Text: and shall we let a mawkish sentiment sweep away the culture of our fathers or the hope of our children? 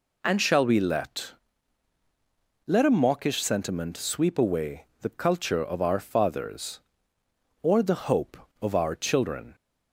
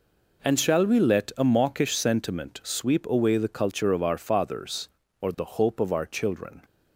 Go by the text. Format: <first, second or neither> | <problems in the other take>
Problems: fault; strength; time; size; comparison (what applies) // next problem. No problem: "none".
second | says "let" twice; at 2.6 s // pauses between "away" and "the"; slight; at 4.8 s; 0.16 s long